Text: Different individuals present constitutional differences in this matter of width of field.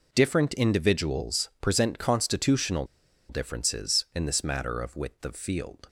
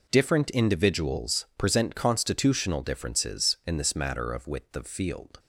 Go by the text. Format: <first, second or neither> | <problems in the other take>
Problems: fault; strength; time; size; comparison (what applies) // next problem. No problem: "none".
second | pauses between "constitutional" and "differences"; at 2.8 s; 0.44 s long